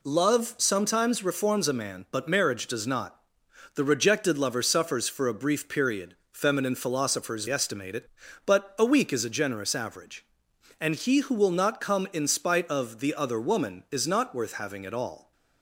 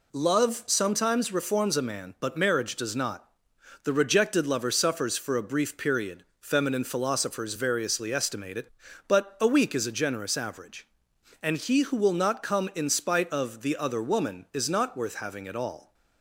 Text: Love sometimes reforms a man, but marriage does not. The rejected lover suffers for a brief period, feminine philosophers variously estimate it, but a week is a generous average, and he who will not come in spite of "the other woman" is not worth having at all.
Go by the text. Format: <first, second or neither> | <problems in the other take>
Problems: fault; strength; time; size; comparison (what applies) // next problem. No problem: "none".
second | skips "variously"; at 7.4 s